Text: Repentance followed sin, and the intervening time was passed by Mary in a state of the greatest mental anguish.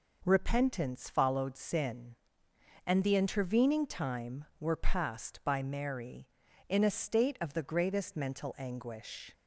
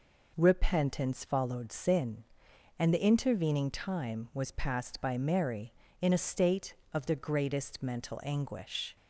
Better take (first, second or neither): second